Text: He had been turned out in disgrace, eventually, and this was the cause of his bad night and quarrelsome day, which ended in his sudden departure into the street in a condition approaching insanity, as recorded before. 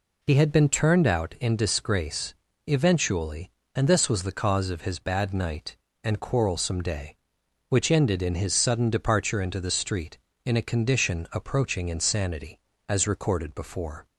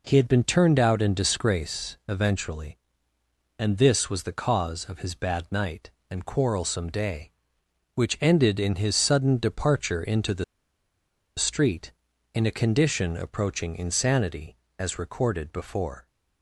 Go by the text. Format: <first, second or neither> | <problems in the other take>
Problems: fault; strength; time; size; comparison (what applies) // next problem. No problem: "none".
first | pauses between "the" and "street"; noticeable; at 10.4 s; 0.93 s long